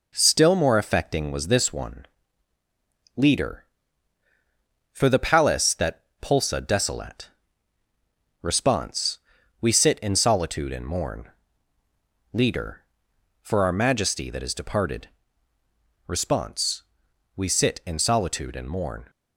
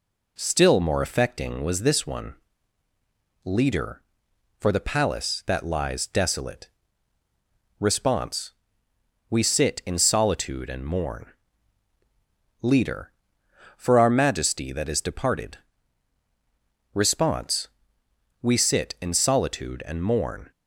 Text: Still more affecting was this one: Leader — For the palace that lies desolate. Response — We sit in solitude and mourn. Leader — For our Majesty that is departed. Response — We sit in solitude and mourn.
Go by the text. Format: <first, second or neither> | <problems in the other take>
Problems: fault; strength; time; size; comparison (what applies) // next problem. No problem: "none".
second | says "pulsa" for "lies"; at 6.2 s